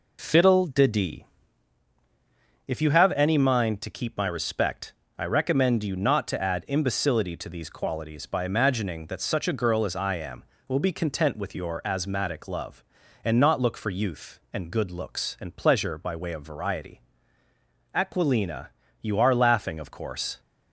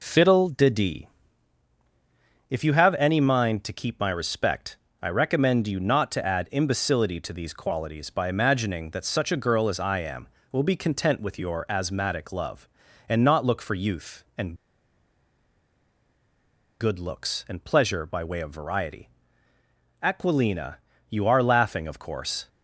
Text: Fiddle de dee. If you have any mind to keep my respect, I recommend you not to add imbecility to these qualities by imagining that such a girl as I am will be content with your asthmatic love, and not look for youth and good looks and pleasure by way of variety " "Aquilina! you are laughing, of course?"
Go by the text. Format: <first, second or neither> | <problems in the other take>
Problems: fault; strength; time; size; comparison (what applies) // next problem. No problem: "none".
first | pauses between "and" and "good"; strong; at 14.5 s; 2.2 s long